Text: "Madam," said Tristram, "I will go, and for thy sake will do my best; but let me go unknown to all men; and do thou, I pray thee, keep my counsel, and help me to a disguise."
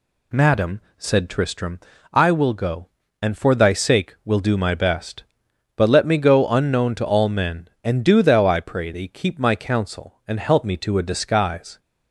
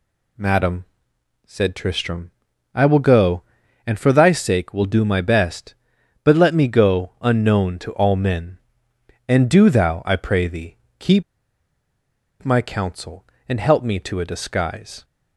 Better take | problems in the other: first | pauses between "keep" and "my"; at 11.2 s; 1.1 s long

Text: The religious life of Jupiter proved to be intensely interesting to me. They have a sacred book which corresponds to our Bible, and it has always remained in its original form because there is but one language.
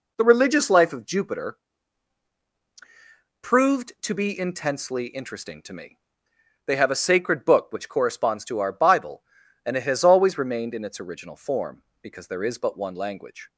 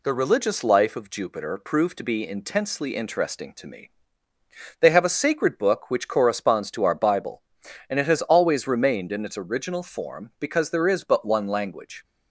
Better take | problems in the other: second | starts louder than the rest; until 1.3 s; 3.5 dB // pauses between "Jupiter" and "proved"; strong; at 1.5 s; 1.8 s long

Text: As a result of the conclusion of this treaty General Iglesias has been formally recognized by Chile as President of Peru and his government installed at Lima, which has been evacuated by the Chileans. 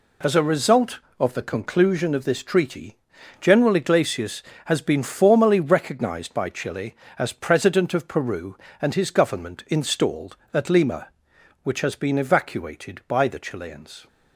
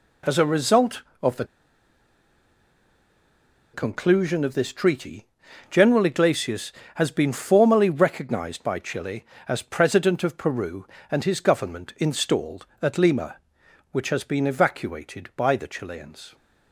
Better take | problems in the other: first | pauses between "the" and "conclusion"; strong; at 1.4 s; 2.2 s long // pauses between "treaty" and "General"; at 5.2 s; 0.44 s long; also in the first

